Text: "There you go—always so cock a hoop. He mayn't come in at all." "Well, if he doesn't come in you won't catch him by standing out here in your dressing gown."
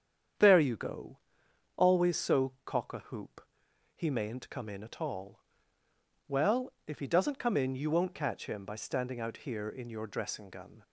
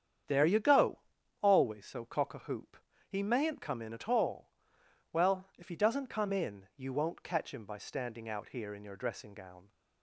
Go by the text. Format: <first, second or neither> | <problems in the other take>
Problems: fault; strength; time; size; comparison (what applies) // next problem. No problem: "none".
second | starts louder than the rest; strong; until 2.0 s; 8 dB; strong in the second // says "gun" for "gown"; at 10.4 s